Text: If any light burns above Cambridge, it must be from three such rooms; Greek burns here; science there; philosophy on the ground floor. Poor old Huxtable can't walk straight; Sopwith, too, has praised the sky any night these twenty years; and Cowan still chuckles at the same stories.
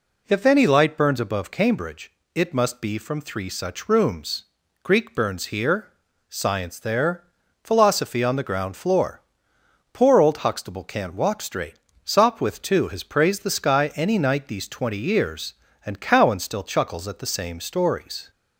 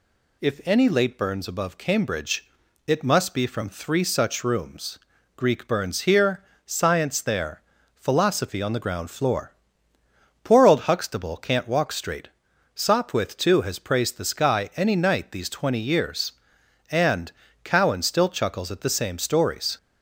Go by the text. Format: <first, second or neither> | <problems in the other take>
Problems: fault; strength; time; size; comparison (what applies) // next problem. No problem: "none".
first | says "late" for "light"; at 0.8 s // pauses between "and" and "Cowan"; slight; at 17.3 s; 0.32 s long